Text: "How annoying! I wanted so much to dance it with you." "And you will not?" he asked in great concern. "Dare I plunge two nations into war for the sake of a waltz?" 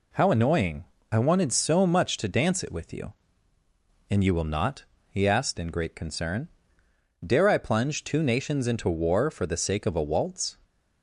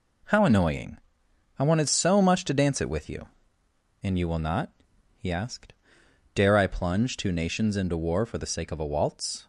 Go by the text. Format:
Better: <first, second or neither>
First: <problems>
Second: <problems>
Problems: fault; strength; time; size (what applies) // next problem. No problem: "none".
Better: first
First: none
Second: skips "in great concern"; at 6.0 s